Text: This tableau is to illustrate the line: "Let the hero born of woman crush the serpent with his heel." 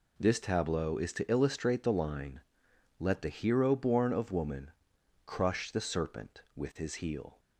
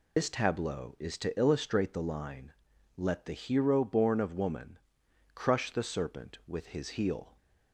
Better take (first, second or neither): first